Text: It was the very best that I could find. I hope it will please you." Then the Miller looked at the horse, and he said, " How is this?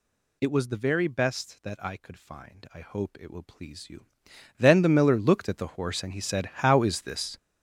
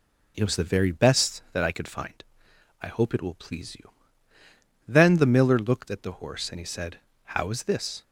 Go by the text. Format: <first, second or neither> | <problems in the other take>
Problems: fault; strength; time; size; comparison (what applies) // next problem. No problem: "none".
second | gets louder; strong; throughout; 11.5 dB